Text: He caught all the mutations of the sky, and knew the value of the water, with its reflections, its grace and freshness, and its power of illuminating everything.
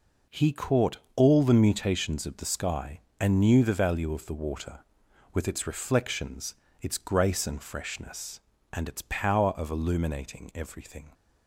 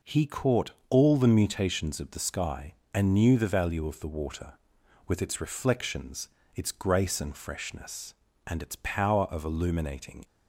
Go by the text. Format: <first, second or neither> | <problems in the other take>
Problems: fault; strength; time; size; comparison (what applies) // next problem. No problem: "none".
first | pauses between "caught" and "all"; slight; at 0.7 s; 0.18 s long; slight in the first // stops before "everything"; at 10.2 s